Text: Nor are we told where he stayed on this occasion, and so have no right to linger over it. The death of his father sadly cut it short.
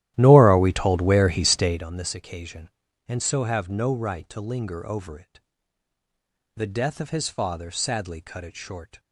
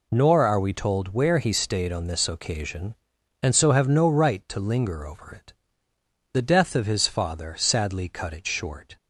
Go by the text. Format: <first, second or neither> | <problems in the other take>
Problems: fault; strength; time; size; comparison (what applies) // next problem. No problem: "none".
second | starts louder than the rest; strong; until 1.8 s; 13 dB